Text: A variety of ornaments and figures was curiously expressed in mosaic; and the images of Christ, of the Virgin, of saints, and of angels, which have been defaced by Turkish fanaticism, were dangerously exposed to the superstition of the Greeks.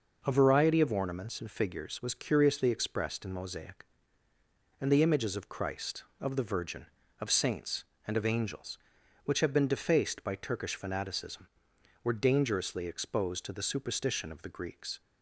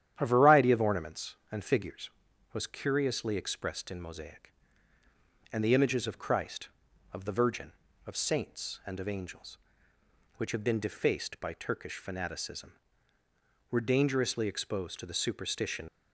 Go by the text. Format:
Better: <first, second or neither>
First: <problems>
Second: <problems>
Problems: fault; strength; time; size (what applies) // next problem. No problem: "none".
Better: first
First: none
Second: starts louder than the rest; strong; until 1.1 s; 10.5 dB // stops before "of the Greeks"; at 15.8 s